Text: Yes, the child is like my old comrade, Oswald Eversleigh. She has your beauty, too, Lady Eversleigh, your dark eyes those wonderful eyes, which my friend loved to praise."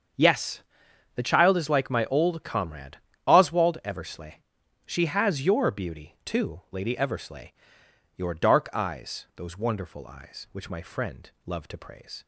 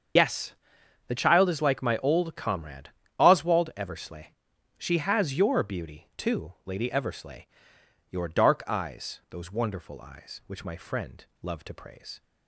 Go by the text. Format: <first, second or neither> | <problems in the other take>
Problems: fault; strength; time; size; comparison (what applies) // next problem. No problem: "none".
first | loses the start of "Yes"; at 0.1 s; 80 ms // starts louder than the rest; strong; until 1.7 s; 7 dB; also in the first // pauses between "friend" and "loved"; slight; at 11.2 s; 0.17 s long; slight in the first